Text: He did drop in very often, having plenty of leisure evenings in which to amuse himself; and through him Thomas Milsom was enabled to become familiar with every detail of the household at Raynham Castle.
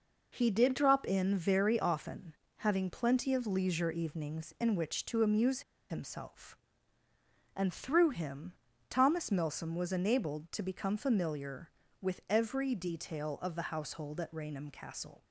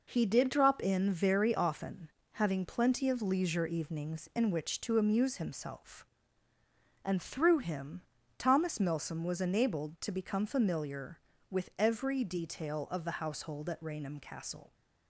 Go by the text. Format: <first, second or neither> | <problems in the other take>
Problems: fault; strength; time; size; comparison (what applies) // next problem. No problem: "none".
second | pauses between "amuse" and "himself"; slight; at 5.6 s; 0.28 s long // pauses between "him" and "Thomas"; at 8.5 s; 0.38 s long; also in the second